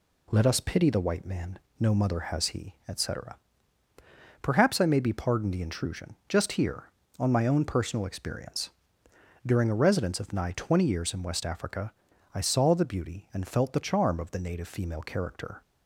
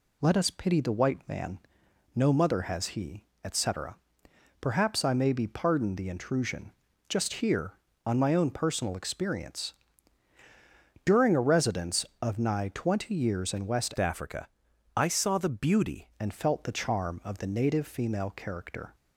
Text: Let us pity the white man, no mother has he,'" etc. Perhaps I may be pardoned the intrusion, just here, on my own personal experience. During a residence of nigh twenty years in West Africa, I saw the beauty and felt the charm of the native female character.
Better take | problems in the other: first | changes voice from "Africa" to "beauty"; from 13.9 to 16.1 s; 2.2 s long

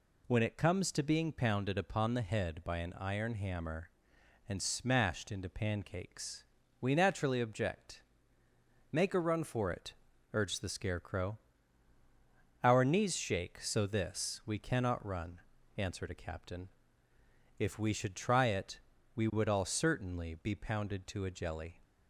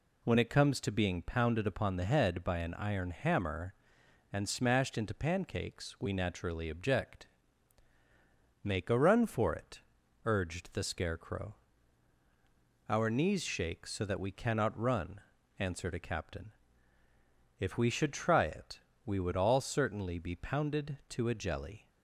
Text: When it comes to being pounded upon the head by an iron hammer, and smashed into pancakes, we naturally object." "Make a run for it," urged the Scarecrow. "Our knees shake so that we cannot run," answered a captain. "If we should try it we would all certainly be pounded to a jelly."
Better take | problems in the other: second | says "this" for "that"; at 13.8 s // pauses between "it" and "we"; slight; at 18.7 s; 0.34 s long; slight in the second

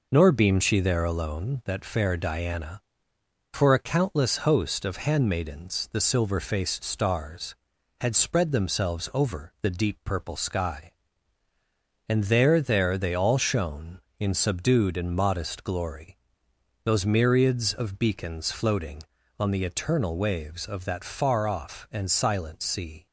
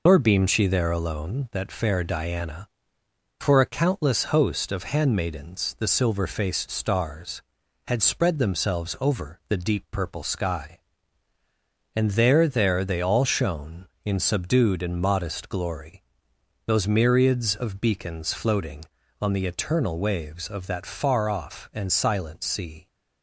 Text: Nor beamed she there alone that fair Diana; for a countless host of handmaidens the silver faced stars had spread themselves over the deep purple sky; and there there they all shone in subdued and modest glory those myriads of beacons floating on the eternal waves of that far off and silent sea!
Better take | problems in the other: first | loses the start of "Nor"; at 0.0 s; 85 ms // pauses between "glory" and "those"; noticeable; at 16.0 s; 0.64 s long; noticeable in the first

